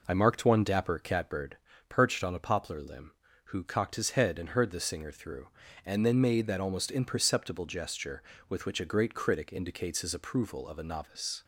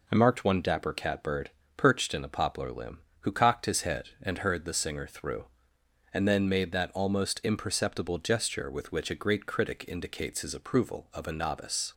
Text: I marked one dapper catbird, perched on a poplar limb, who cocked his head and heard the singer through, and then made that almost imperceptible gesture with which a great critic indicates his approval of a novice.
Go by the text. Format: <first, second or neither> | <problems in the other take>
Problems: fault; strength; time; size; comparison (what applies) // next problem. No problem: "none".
first | says "in" for "on"; at 2.1 s